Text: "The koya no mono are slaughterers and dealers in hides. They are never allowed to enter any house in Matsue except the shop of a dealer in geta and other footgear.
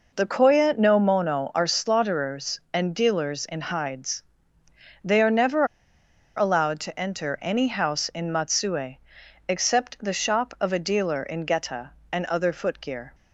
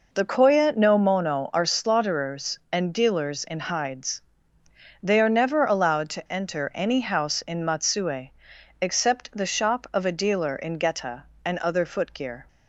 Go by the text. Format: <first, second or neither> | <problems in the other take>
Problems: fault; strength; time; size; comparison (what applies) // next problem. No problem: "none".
second | pauses between "never" and "allowed"; noticeable; at 5.6 s; 0.71 s long // pauses between "Matsue" and "except"; noticeable; at 8.9 s; 0.52 s long; noticeable in the second